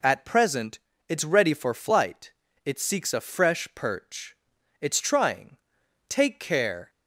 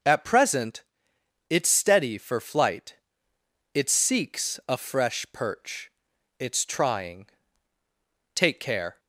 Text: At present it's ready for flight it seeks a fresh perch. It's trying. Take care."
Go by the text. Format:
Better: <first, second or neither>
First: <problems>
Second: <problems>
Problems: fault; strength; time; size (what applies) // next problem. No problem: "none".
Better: first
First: pauses between "present" and "it's"; slight; at 0.7 s; 0.28 s long // pauses between "flight" and "it"; slight; at 2.3 s; 0.32 s long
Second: pauses between "present" and "it's"; noticeable; at 0.8 s; 0.67 s long // says "steady" for "ready"; at 1.6 s // pauses between "flight" and "it"; noticeable; at 2.9 s; 0.78 s long